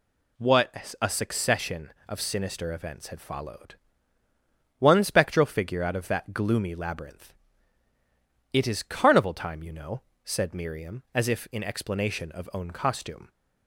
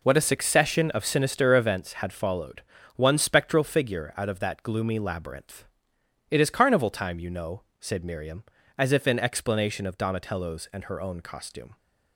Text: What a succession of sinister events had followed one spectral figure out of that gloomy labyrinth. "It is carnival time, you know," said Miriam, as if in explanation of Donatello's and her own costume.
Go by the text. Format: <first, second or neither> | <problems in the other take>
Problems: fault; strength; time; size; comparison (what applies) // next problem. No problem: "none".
second | pauses between "followed" and "one"; at 3.7 s; 1.0 s long; slight in the second // skips "Donatello's and her"; at 12.5 s